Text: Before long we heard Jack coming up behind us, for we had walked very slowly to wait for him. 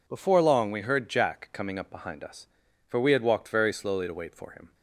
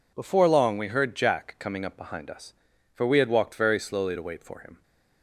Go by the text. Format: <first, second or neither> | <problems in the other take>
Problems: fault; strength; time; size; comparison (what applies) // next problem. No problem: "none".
neither | none